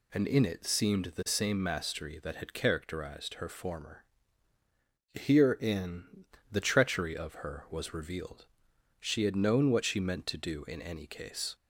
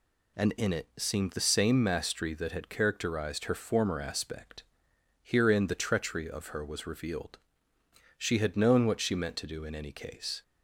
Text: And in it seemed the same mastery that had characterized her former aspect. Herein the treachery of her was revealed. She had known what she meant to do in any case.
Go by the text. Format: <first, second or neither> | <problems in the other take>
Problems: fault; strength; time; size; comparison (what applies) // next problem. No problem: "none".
second | skips "aspect"; at 4.5 s // pauses between "Herein" and "the"; slight; at 6.2 s; 0.26 s long